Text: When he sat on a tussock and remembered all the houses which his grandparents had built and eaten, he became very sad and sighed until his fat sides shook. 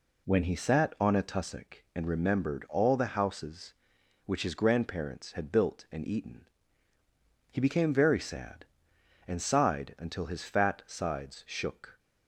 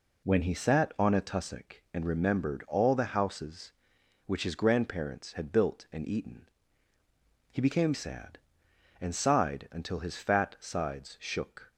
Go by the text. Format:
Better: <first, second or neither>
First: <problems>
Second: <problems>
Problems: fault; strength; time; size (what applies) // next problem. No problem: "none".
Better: first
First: none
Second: skips "very"; at 7.9 s